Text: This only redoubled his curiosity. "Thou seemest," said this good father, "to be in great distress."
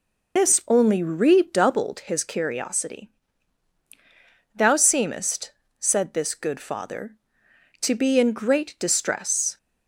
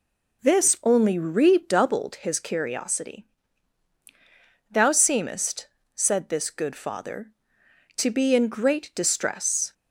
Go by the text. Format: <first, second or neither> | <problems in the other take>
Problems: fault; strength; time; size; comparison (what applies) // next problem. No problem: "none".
second | loses the start of "This"; at 0.3 s; 105 ms